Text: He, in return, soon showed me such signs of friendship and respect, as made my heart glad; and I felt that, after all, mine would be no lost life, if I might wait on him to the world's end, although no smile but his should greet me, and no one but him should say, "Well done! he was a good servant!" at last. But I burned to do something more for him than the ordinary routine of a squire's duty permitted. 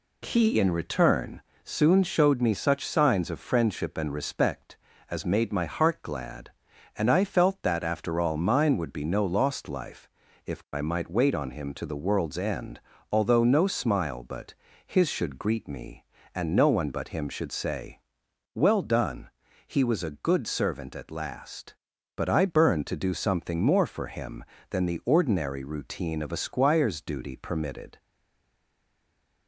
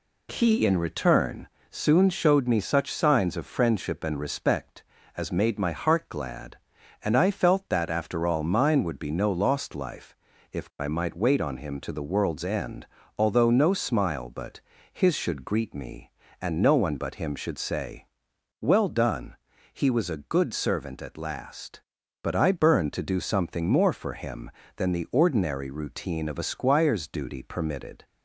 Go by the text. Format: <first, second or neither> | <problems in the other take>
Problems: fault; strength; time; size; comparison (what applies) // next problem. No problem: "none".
second | pauses between "but" and "his"; slight; at 14.5 s; 0.32 s long; slight in the second // stays silent after the last word; noticeable; from 27.9 s on; 1.5 s long